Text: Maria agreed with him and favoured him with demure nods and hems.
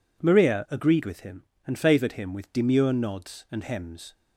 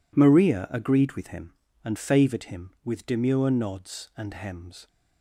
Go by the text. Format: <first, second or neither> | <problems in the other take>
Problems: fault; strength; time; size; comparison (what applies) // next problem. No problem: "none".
neither | none